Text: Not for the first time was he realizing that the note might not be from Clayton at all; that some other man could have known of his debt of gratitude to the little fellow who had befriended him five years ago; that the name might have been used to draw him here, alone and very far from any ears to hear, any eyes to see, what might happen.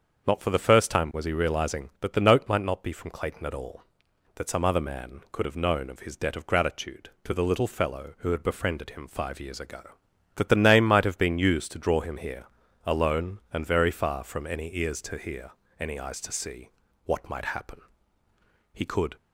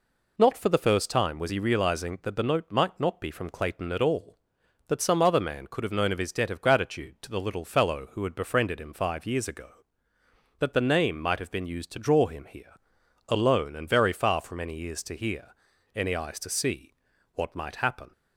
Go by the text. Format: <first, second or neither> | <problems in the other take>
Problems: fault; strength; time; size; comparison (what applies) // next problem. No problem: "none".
second | starts louder than the rest; until 1.3 s; 7 dB // goes on to say "He could"; slight; from 18.7 s on; 0.44 s long